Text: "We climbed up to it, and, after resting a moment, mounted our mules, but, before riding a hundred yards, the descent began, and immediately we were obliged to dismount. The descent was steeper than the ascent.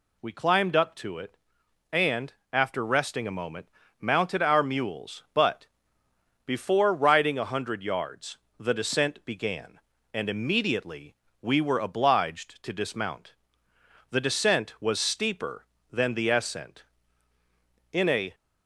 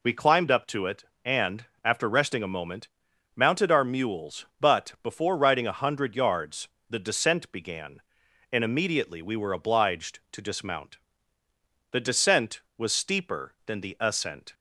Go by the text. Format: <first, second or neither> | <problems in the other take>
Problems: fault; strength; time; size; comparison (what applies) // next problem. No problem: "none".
second | pauses between "immediately" and "we"; slight; at 11.1 s; 0.26 s long // goes on to say "In a"; slight; from 17.9 s on; 0.42 s long